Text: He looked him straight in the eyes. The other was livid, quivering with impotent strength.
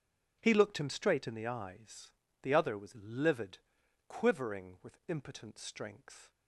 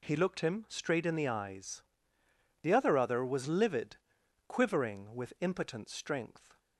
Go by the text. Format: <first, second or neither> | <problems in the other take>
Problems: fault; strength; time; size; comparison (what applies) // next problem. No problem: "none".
first | says "other" twice; at 2.9 s